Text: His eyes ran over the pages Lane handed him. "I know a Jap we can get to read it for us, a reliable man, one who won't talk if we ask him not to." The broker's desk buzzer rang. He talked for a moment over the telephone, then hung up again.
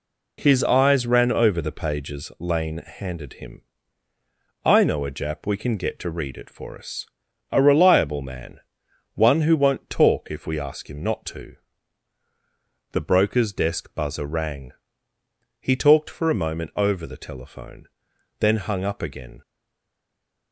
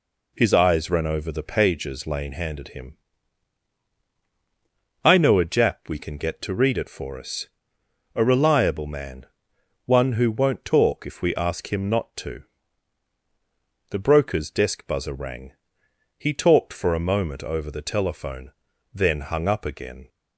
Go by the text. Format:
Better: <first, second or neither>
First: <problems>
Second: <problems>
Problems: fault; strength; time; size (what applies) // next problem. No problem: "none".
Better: second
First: stays silent after the last word; from 19.4 s on; 1.1 s long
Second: none